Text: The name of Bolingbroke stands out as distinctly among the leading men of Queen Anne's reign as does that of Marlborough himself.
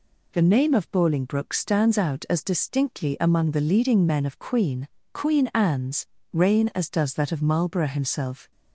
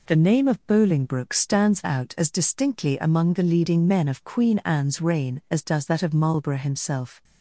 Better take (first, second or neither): second